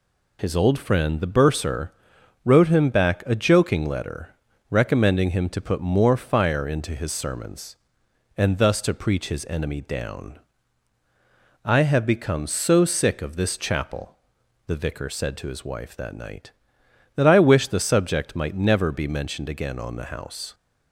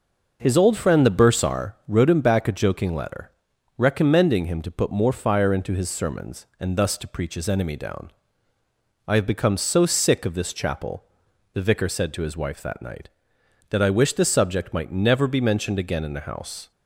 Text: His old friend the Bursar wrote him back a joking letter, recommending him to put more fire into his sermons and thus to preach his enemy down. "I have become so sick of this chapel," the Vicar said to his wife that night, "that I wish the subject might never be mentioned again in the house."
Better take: second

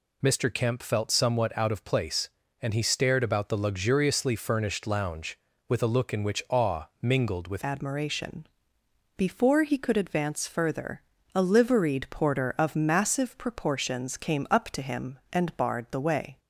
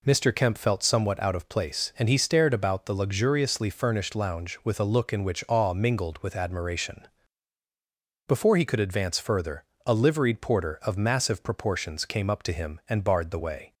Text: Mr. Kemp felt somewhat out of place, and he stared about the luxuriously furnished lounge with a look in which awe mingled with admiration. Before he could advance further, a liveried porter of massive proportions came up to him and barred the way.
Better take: second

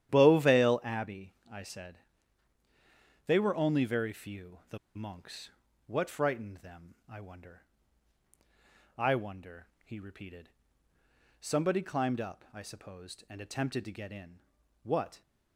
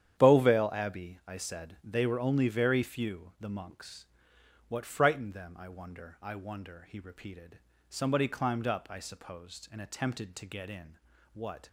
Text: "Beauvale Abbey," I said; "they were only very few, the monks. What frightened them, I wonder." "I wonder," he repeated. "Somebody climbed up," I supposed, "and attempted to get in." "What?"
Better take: second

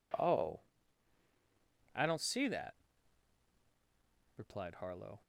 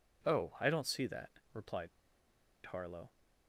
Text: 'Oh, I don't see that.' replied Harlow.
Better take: first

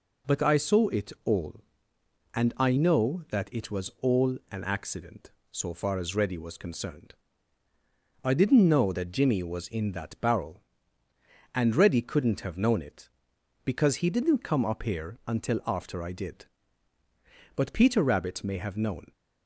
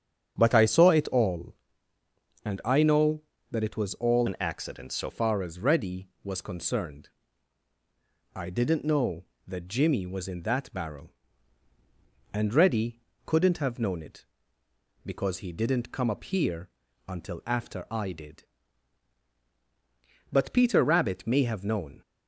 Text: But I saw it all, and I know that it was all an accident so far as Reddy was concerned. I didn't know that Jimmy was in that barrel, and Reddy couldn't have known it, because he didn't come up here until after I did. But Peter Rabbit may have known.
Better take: first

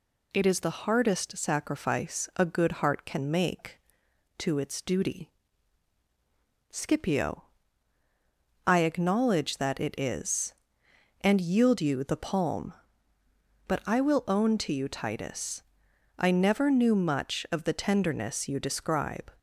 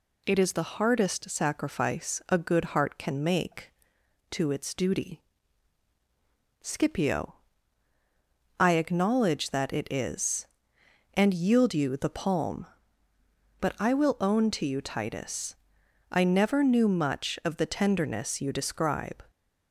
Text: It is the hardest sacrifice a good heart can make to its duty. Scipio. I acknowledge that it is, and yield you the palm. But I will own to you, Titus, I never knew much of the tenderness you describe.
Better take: neither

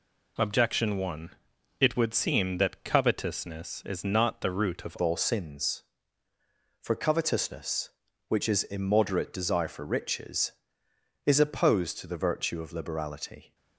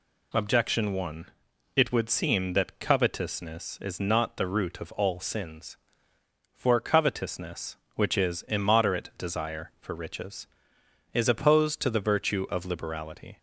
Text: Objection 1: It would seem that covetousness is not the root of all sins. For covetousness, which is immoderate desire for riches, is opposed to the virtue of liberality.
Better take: second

